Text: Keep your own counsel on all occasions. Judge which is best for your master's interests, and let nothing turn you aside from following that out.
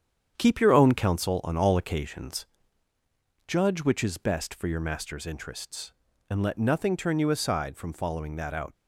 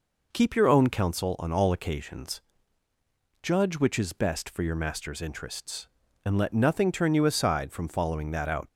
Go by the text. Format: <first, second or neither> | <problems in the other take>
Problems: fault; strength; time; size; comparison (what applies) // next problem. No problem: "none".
second | gets quieter; throughout; 6.5 dB